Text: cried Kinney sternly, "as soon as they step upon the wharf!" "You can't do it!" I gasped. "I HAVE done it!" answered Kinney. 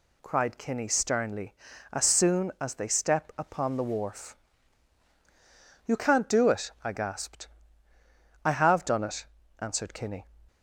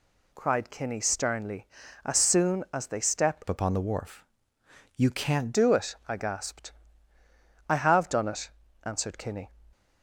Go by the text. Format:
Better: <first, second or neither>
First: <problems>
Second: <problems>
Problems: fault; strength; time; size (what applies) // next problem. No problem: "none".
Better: first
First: none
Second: changes voice from "upon" to "can't"; from 3.4 to 5.5 s; 2.1 s long